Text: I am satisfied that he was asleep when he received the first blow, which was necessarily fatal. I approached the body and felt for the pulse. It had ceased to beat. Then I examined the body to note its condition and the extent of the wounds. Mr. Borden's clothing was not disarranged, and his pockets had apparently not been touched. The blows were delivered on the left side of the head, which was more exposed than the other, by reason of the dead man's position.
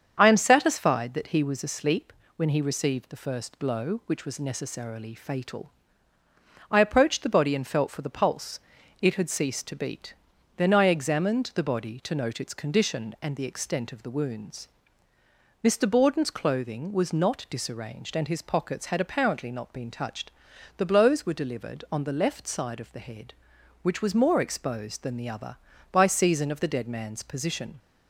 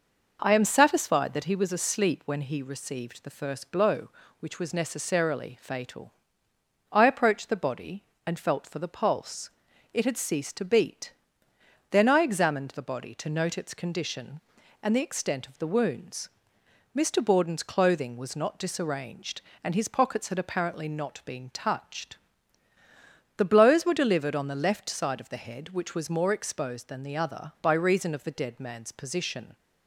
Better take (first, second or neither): second